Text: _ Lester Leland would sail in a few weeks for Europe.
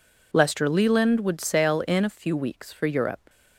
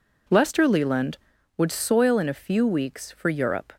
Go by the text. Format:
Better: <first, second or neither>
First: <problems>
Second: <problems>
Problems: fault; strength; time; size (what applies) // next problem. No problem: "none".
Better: first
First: none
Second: says "soil" for "sail"; at 1.7 s